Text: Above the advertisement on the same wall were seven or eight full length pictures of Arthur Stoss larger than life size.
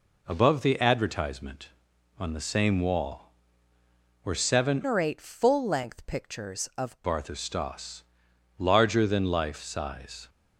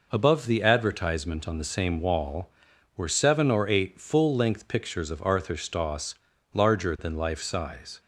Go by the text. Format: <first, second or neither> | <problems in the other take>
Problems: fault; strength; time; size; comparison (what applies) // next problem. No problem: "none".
second | changes voice from "or" to "of"; from 4.8 to 6.9 s; 2.1 s long // pauses between "Stoss" and "larger"; noticeable; at 8.0 s; 0.52 s long; also in the second